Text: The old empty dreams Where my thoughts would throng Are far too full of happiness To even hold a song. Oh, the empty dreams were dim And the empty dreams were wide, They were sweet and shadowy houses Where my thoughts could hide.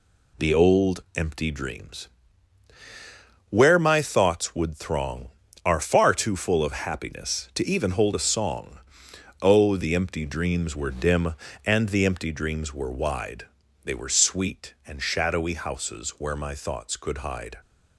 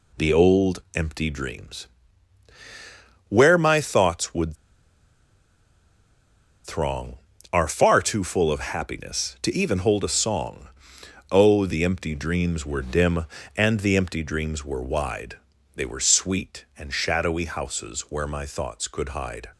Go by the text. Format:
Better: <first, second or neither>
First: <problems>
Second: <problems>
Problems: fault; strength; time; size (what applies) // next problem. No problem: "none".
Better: first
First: pauses between "dreams" and "Where"; strong; at 2.0 s; 1.4 s long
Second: pauses between "dreams" and "Where"; strong; at 1.8 s; 1.4 s long // pauses between "would" and "throng"; strong; at 4.5 s; 2.1 s long